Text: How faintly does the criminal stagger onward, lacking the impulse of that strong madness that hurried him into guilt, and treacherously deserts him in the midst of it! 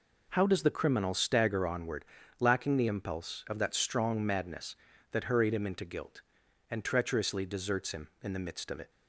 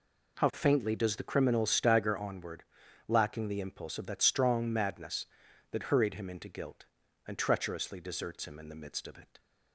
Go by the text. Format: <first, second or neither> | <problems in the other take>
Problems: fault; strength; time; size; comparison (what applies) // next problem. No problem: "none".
second | skips "faintly"; at 0.4 s